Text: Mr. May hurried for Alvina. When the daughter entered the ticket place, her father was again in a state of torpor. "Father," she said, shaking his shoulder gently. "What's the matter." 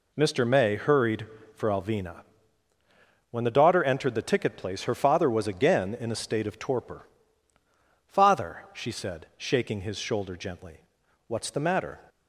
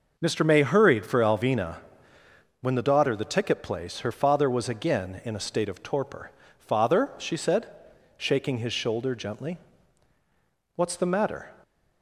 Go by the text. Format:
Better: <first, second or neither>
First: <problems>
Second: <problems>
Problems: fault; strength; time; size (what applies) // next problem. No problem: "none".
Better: first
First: none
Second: skips "entered"; at 3.1 s